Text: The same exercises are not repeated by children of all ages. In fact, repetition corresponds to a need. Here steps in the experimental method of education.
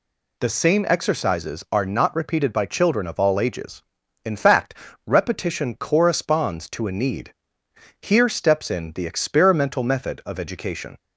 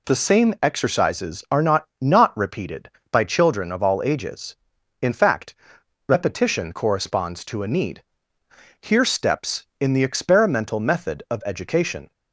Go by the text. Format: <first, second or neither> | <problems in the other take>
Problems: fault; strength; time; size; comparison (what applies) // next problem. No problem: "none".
first | says "not" twice; at 1.9 s